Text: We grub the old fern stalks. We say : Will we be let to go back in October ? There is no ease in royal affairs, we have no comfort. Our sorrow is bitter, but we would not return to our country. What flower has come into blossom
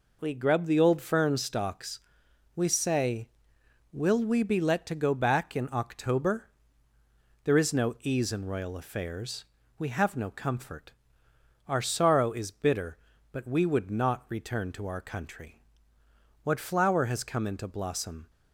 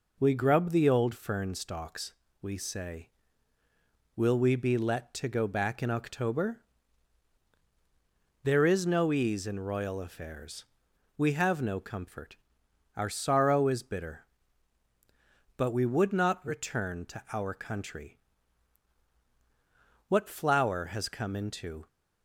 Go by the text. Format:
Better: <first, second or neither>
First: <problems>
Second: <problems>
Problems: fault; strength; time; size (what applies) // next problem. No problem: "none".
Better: first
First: none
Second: stops before "blossom"; at 21.8 s